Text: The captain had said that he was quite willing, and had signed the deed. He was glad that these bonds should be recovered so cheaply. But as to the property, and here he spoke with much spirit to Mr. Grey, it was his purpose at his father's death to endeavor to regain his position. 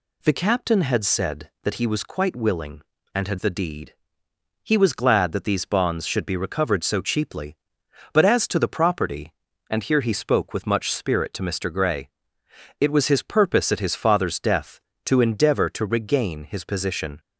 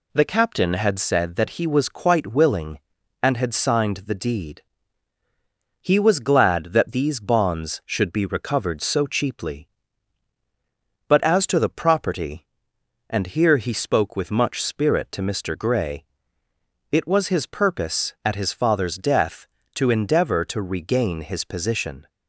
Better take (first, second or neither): second